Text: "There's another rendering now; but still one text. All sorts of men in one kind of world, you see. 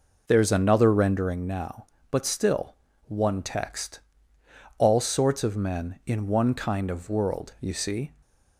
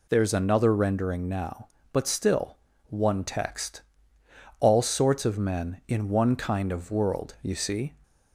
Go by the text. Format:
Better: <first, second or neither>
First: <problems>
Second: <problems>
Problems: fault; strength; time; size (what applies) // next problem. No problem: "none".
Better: second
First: starts louder than the rest; noticeable; until 1.4 s; 5 dB // pauses between "still" and "one"; slight; at 2.7 s; 0.32 s long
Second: pauses between "still" and "one"; slight; at 2.5 s; 0.32 s long